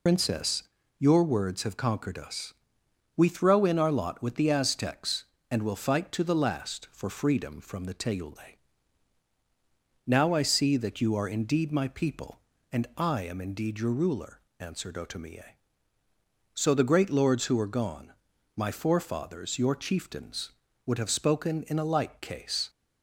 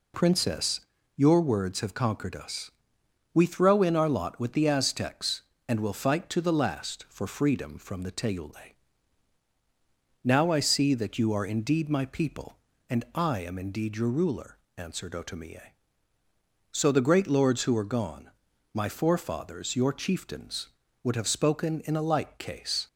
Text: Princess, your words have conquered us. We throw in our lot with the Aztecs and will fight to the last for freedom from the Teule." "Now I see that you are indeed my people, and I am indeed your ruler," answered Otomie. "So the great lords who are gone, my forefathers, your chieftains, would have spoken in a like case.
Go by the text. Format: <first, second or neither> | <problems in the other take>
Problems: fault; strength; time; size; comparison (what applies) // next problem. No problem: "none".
second | loses the start of "Princess"; at 0.0 s; 90 ms